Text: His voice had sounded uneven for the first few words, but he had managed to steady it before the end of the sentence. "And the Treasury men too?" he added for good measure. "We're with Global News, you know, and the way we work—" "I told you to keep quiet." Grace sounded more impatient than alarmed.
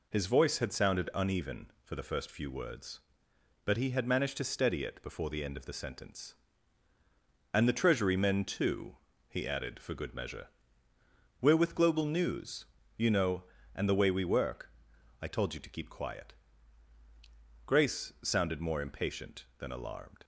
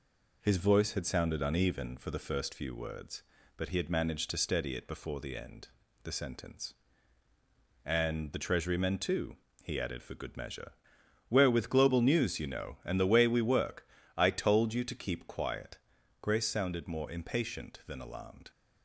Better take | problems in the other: first | skips "of"; at 5.8 s

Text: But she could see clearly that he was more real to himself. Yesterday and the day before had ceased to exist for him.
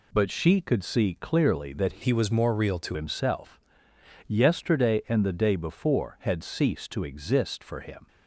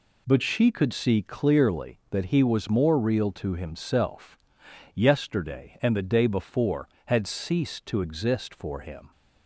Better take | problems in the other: second | changes voice from "he" to "to"; from 2.0 to 2.9 s; 0.9 s long

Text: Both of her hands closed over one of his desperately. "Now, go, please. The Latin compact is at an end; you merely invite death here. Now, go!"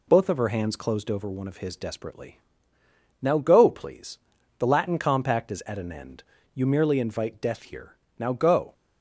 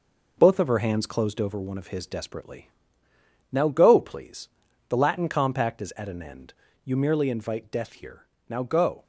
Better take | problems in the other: first | gets quieter; noticeable; throughout; 4.5 dB

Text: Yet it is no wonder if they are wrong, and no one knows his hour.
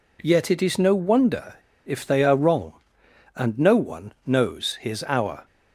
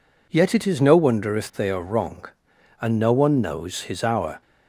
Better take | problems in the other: second | pauses between "wonder" and "if"; slight; at 1.5 s; 0.31 s long

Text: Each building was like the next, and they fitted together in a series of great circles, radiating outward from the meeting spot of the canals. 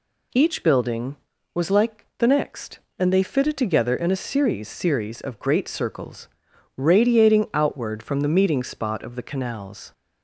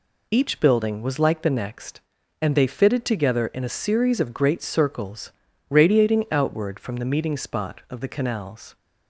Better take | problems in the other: second | says "series" twice; at 4.6 s

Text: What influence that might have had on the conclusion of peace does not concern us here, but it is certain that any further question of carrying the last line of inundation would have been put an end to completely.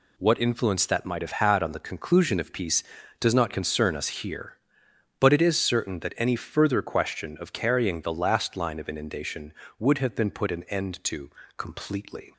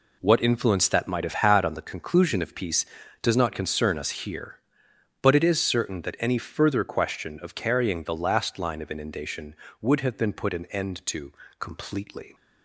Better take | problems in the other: first | starts louder than the rest; slight; until 1.7 s; 3 dB // pauses between "to" and "completely"; slight; at 11.3 s; 0.30 s long; slight in the first

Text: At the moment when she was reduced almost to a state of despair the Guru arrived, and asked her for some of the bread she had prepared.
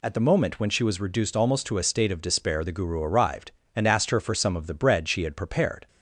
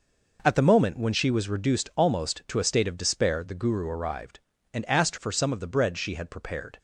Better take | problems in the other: first | skips "her"; at 5.1 s

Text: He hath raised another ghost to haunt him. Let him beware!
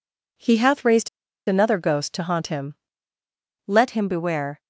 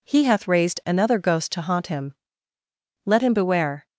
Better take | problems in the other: second | pauses between "raised" and "another"; at 1.0 s; 0.39 s long

